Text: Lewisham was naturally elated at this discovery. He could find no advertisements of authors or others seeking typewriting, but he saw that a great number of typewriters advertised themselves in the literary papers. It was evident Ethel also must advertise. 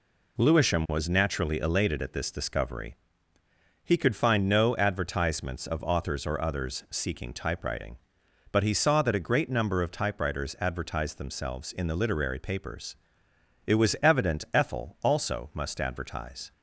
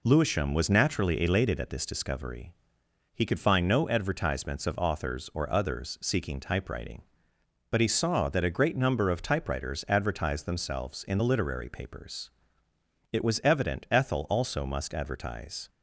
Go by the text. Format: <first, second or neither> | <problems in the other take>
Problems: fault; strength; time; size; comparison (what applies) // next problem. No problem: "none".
neither | none